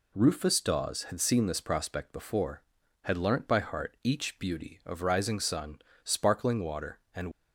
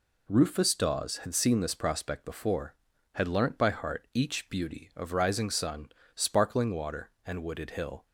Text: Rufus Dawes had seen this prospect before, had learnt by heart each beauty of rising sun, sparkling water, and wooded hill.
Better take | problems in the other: second | stops before "wooded hill"; at 7.3 s

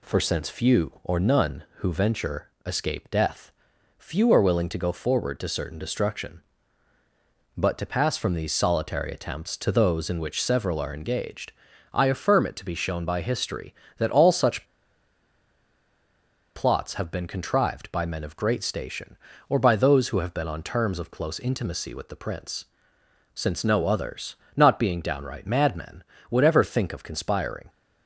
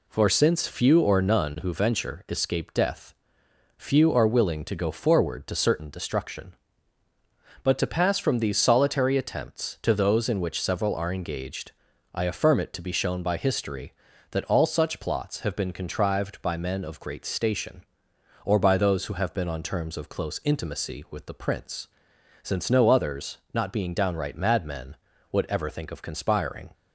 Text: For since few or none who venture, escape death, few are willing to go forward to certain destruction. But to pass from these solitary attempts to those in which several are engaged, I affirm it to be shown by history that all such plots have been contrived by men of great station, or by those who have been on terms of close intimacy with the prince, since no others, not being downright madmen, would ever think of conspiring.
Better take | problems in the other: second | pauses between "such" and "plots"; strong; at 14.6 s; 1.9 s long

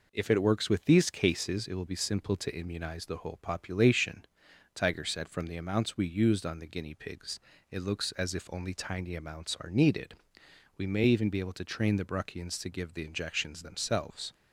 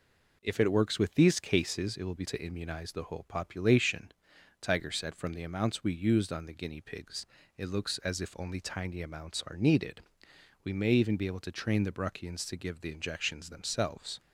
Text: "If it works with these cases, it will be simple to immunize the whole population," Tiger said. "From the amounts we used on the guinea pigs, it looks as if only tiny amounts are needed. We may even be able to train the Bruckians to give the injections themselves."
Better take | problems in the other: first | skips "simple"; at 2.2 s

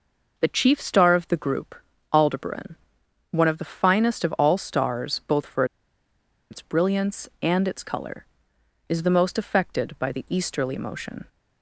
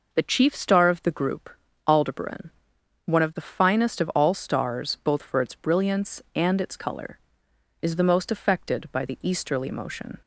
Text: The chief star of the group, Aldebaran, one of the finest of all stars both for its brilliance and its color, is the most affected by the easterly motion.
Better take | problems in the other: second | pauses between "for" and "its"; noticeable; at 5.6 s; 0.86 s long

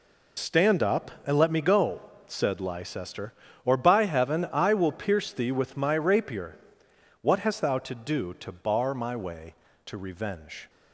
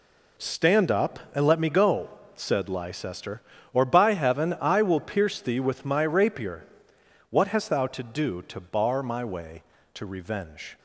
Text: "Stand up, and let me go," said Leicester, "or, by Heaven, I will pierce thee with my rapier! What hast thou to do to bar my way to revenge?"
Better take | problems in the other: second | loses the start of "Stand"; at 0.3 s; 75 ms

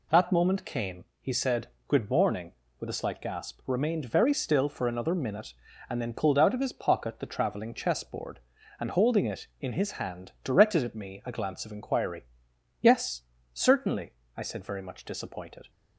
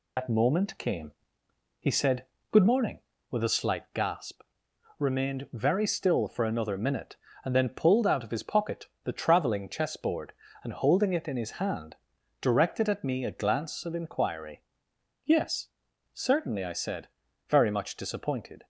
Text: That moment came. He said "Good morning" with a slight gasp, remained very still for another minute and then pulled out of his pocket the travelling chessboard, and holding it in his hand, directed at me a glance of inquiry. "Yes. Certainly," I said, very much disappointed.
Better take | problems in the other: first | loses the start of "That"; at 0.1 s; 90 ms // pauses between "said" and "Good"; slight; at 2.2 s; 0.26 s long; slight in the first // pauses between "pocket" and "the"; slight; at 8.8 s; 0.18 s long

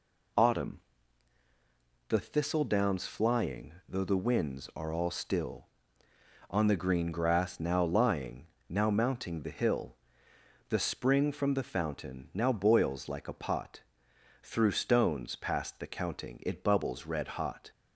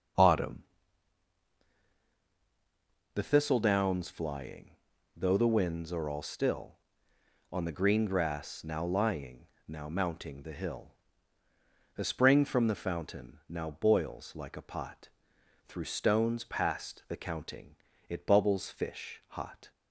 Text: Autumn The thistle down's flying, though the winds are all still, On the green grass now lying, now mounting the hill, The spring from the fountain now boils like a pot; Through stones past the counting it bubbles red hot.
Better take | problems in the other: first | starts louder than the rest; until 3.6 s; 6.5 dB // pauses between "Autumn" and "The"; strong; at 0.6 s; 2.5 s long; strong in the first // pauses between "counting" and "it"; slight; at 17.7 s; 0.32 s long // says "fish" for "red"; at 18.6 s

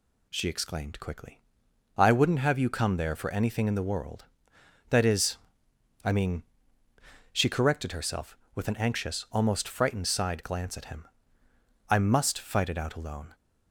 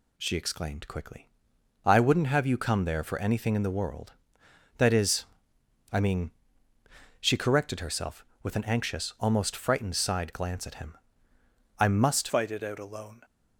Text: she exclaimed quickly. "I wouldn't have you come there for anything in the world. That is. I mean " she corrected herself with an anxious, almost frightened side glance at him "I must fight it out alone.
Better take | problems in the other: first | pauses between "him" and "I"; noticeable; at 10.9 s; 0.84 s long; noticeable in the first // changes voice at "fight"; from 12.2 s on; 1.0 s long

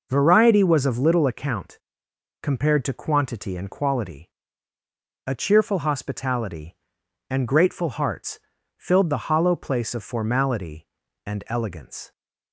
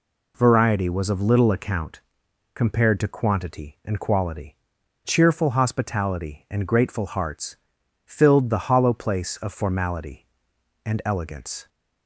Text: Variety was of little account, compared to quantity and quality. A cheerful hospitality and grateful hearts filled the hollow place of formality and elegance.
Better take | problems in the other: first | skips "A"; at 4.8 s // pauses between "hearts" and "filled"; noticeable; at 7.5 s; 0.50 s long; also in the first

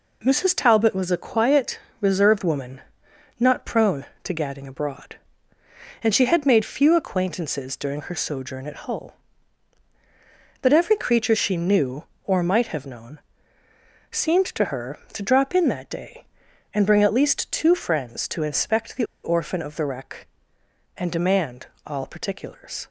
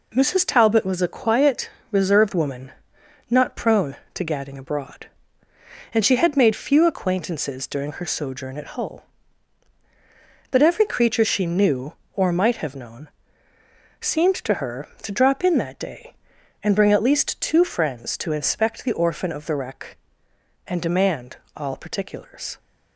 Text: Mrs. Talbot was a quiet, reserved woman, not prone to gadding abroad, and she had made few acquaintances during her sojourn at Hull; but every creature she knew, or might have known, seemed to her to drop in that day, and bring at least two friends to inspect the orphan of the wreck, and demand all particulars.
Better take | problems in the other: second | pauses between "the" and "orphan"; slight; at 19.0 s; 0.17 s long // pauses between "demand" and "all"; slight; at 21.6 s; 0.20 s long; slight in the second

